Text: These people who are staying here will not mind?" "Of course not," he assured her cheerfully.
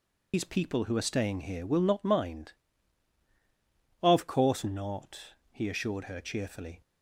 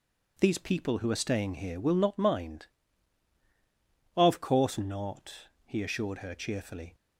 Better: second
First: loses the start of "These"; at 0.3 s; 90 ms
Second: none

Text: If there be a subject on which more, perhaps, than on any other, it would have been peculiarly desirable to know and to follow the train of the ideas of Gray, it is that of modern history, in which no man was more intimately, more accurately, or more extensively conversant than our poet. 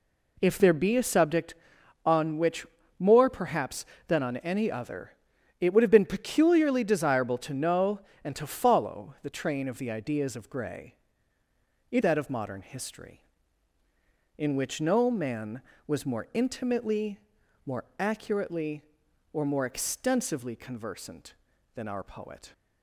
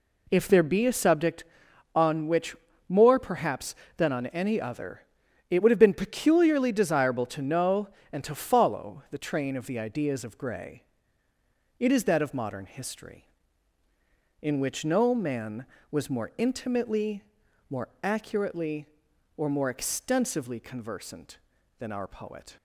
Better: second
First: pauses between "which" and "more"; slight; at 2.6 s; 0.32 s long // skips "is"; at 12.0 s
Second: pauses between "which" and "more"; slight; at 2.5 s; 0.32 s long

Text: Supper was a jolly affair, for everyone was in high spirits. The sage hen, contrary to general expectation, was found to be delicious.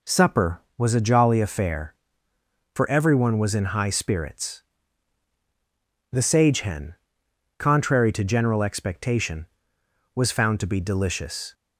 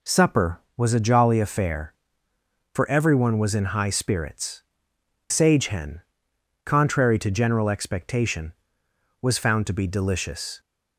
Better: first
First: none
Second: skips "The"; at 4.9 s

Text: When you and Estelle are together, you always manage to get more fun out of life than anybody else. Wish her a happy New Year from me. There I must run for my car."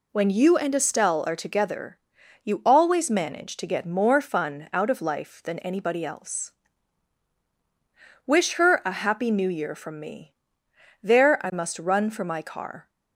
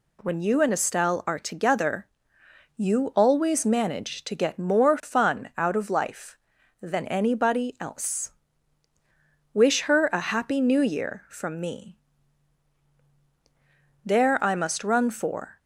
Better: first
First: none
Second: stops before "my car"; at 15.5 s

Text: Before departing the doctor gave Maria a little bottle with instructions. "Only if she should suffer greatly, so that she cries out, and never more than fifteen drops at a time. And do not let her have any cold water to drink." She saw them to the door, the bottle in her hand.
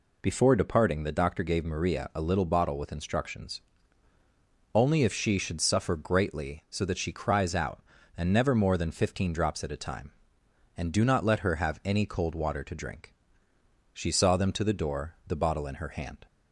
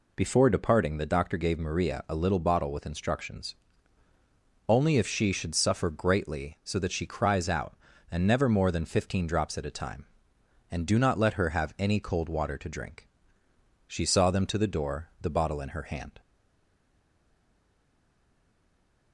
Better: first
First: none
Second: stays silent after the last word; strong; from 16.1 s on; 3.0 s long

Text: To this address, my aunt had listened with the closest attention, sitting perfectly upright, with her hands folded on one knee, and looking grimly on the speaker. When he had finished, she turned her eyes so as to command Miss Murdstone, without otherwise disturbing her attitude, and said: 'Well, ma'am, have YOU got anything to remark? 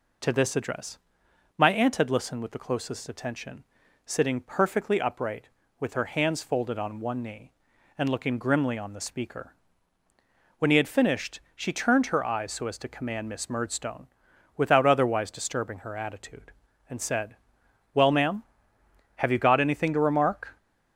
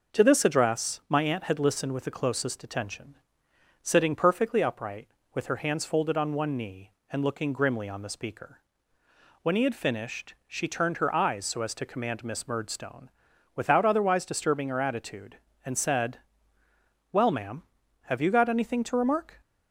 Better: neither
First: none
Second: none

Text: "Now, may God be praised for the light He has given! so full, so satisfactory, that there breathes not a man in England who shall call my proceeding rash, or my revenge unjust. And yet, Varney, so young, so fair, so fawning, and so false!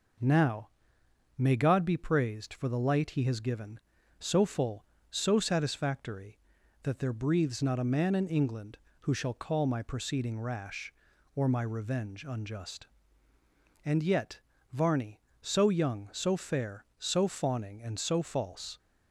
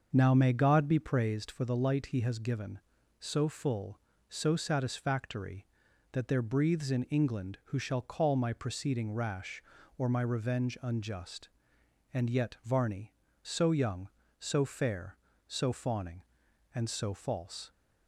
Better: first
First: none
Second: starts louder than the rest; until 1.1 s; 6.5 dB // skips "not a man"; at 6.9 s

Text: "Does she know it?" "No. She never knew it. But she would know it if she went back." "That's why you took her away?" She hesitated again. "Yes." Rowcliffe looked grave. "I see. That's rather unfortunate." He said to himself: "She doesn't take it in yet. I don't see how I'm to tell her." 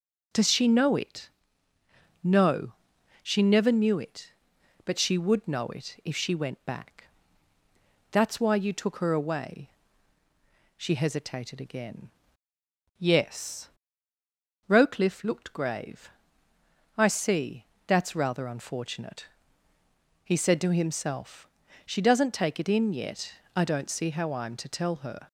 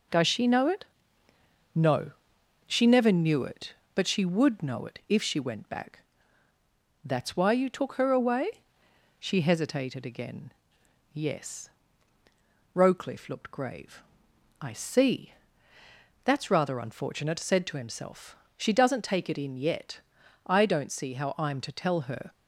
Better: first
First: none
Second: skips "He"; at 17.3 s

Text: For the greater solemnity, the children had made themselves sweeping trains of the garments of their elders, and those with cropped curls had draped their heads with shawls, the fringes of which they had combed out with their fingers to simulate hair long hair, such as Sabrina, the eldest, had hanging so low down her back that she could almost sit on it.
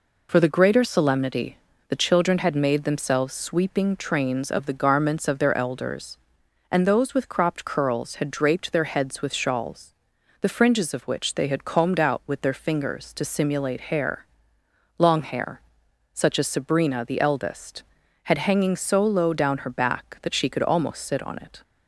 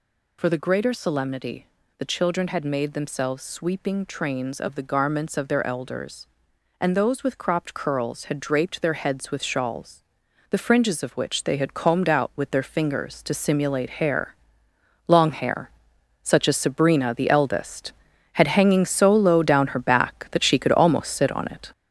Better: first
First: pauses between "hair" and "long"; noticeable; at 14.2 s; 0.74 s long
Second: gets louder; throughout; 6.5 dB // pauses between "hair" and "long"; noticeable; at 14.3 s; 0.74 s long

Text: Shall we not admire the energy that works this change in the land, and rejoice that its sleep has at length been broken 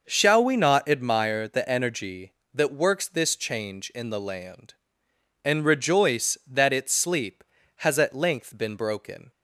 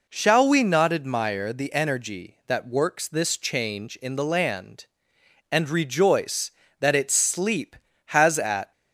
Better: first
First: none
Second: stops before "length been broken"; at 8.7 s

